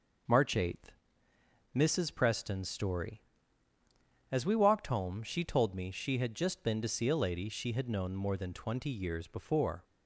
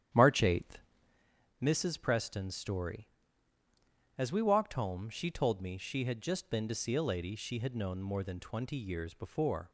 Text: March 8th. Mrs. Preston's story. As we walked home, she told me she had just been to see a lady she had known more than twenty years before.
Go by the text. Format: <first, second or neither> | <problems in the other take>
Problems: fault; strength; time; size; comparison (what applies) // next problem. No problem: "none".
first | starts louder than the rest; strong; until 1.3 s; 10 dB